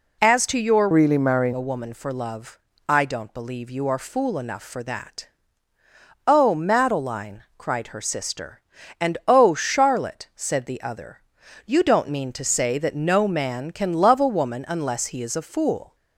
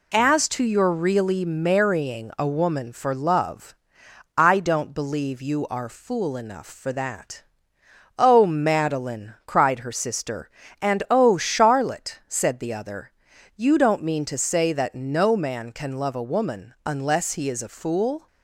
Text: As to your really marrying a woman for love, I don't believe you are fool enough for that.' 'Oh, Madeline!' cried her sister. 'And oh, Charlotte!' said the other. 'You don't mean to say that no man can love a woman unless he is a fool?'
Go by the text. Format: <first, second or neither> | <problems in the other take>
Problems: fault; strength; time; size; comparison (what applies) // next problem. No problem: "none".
second | changes voice from "really" to "marrying"; from 0.9 to 1.5 s; 0.6 s long